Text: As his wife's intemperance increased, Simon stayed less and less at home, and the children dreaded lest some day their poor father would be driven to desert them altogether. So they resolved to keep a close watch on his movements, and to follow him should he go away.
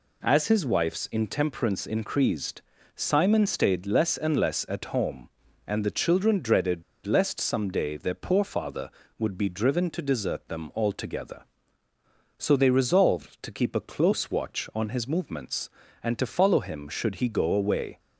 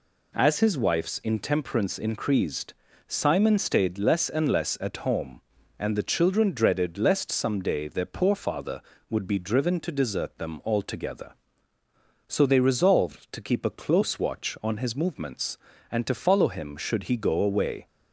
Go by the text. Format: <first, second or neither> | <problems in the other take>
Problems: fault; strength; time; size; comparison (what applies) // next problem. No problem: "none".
second | pauses between "dreaded" and "lest"; slight; at 6.8 s; 0.23 s long